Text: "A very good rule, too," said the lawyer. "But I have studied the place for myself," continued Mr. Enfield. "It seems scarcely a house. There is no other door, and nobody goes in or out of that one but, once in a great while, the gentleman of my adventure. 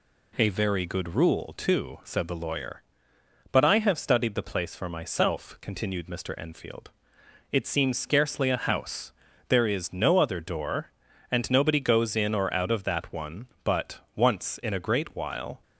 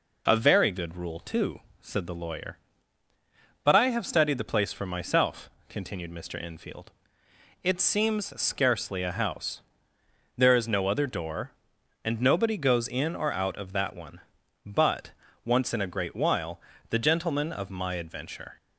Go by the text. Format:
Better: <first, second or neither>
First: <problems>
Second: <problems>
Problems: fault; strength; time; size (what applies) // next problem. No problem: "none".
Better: second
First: stops before "the gentleman of my adventure"; at 15.6 s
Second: none